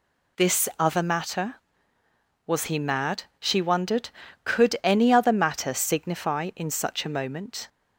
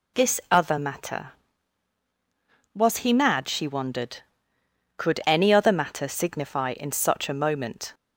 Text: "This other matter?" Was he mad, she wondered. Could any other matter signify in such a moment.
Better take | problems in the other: neither | none

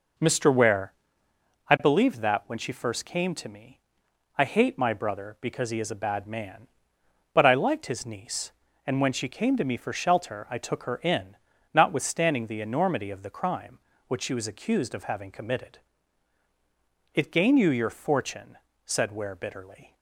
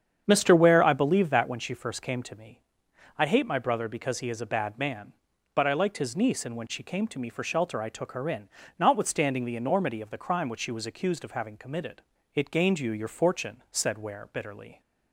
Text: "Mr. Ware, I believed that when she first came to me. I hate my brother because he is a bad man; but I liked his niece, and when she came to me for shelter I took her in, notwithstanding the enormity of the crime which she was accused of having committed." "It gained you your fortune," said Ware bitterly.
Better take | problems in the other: first | starts louder than the rest; strong; until 1.6 s; 8 dB

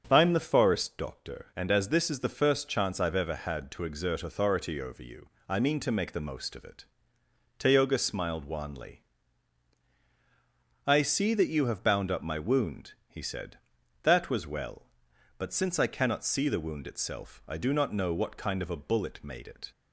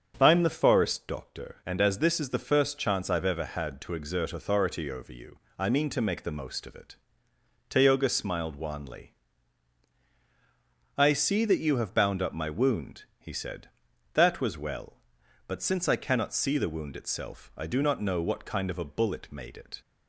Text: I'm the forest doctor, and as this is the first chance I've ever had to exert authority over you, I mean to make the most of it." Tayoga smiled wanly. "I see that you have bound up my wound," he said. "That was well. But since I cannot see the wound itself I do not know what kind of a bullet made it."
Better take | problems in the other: neither | starts louder than the rest; the same in both

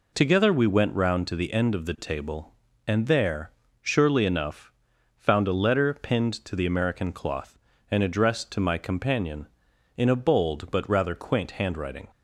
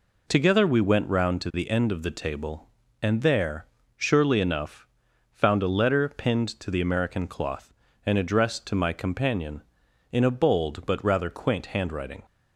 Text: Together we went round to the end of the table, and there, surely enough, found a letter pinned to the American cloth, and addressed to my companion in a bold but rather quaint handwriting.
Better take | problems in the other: neither | none

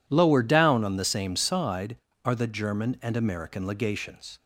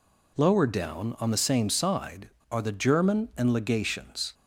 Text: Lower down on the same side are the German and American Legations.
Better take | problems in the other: first | skips "American"; at 3.5 s

